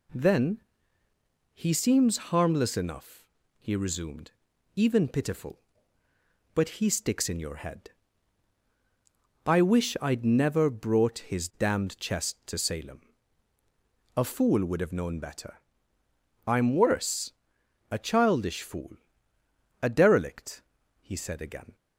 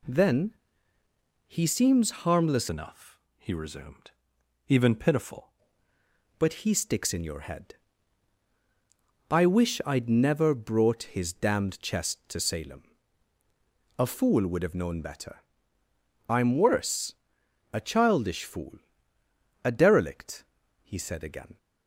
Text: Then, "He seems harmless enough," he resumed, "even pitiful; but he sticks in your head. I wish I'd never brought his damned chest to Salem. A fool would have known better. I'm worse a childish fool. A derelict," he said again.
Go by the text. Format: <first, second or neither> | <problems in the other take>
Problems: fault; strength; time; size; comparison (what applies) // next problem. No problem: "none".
first | changes voice from "enough" to "pitiful"; from 2.7 to 5.5 s; 2.8 s long // pauses between "worse" and "a"; noticeable; at 17.1 s; 0.60 s long; noticeable in the first